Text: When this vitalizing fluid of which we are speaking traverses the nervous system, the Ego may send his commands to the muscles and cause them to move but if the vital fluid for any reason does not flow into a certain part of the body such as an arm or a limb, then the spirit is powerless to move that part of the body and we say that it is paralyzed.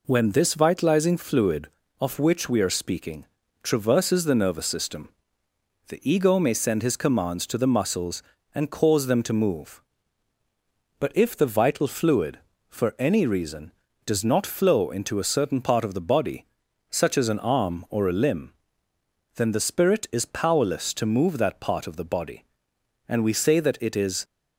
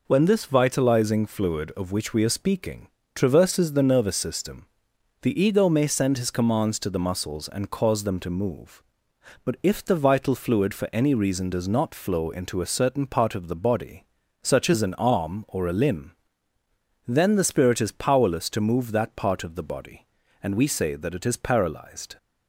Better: second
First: pauses between "speaking" and "traverses"; at 3.2 s; 0.38 s long // pauses between "body" and "such"; at 16.4 s; 0.44 s long // stops before "paralyzed"; at 24.2 s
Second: pauses between "speaking" and "traverses"; slight; at 2.8 s; 0.26 s long // pauses between "body" and "such"; slight; at 14.0 s; 0.36 s long

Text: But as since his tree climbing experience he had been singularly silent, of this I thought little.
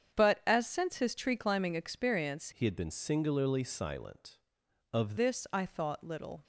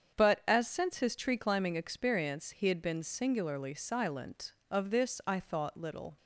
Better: second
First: starts louder than the rest; strong; until 1.2 s; 8 dB // changes voice from "he" to "of"; from 2.5 to 5.1 s; 2.6 s long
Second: starts louder than the rest; strong; until 1.2 s; 7.5 dB

